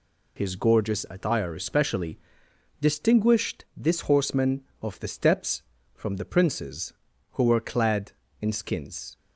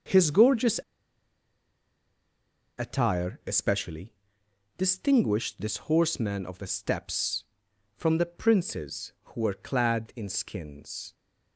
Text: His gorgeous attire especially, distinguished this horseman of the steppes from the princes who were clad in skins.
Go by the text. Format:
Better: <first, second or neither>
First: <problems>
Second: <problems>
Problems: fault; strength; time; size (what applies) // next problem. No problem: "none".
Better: first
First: none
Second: starts louder than the rest; noticeable; until 3.0 s; 6 dB // pauses between "gorgeous" and "attire"; strong; at 0.7 s; 2.0 s long